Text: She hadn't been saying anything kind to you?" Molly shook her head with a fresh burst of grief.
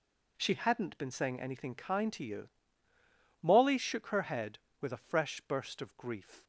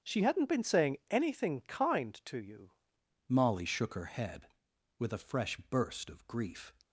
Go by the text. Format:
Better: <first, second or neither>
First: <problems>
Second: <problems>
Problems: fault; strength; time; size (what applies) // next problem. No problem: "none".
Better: first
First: none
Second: starts louder than the rest; strong; until 1.1 s; 7.5 dB // changes voice at "Molly"; from 3.2 s on; 3.5 s long